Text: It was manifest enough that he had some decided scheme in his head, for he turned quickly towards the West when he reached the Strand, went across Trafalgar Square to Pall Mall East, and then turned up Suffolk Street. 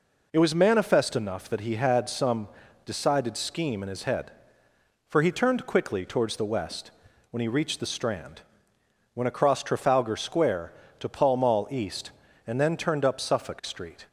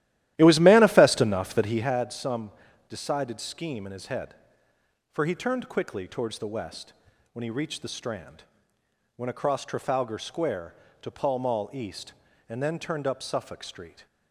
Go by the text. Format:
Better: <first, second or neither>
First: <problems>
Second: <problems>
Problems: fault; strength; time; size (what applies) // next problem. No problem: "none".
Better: first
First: pauses between "some" and "decided"; slight; at 2.4 s; 0.36 s long // pauses between "West" and "when"; at 6.8 s; 0.40 s long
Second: starts louder than the rest; strong; until 2.0 s; 14 dB // pauses between "some" and "decided"; slight; at 2.5 s; 0.36 s long // pauses between "West" and "when"; at 6.9 s; 0.40 s long